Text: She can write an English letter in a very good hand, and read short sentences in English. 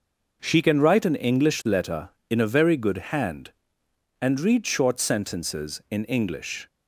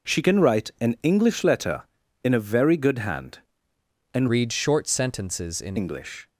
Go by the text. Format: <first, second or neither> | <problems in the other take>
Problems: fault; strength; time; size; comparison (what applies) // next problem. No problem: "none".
first | changes voice from "read" to "in"; from 4.2 to 5.7 s; 1.5 s long